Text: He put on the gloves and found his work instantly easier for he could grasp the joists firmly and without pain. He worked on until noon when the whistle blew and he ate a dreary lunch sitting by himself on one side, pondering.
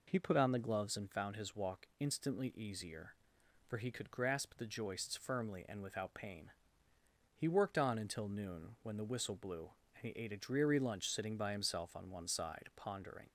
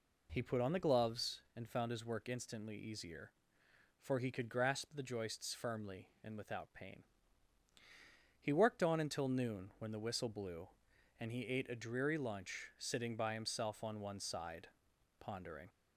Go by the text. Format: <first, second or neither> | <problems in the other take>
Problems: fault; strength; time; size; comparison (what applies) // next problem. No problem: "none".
second | says "walk" for "work"; at 1.5 s